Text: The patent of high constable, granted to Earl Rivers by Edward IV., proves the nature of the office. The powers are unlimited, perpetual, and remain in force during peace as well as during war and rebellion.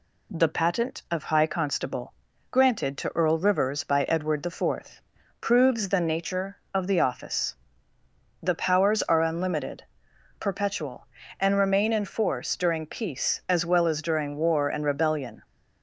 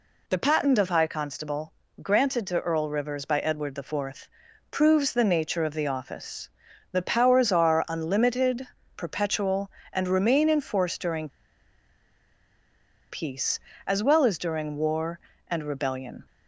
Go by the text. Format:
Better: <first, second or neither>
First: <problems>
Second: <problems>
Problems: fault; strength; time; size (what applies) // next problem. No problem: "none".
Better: first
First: none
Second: pauses between "during" and "peace"; strong; at 11.2 s; 1.8 s long